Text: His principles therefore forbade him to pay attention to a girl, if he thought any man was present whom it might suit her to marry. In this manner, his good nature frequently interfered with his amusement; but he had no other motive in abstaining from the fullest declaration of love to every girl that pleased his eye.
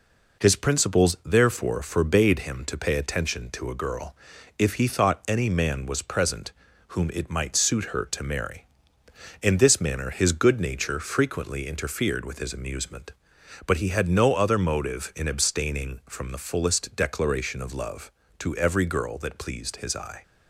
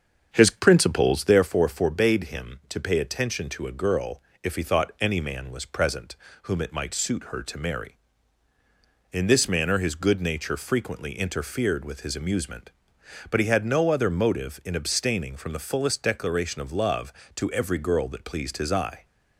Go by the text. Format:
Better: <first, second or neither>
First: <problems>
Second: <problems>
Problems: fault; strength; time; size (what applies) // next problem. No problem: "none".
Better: first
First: pauses between "present" and "whom"; slight; at 6.5 s; 0.36 s long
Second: starts louder than the rest; until 1.5 s; 7 dB // pauses between "present" and "whom"; slight; at 6.1 s; 0.26 s long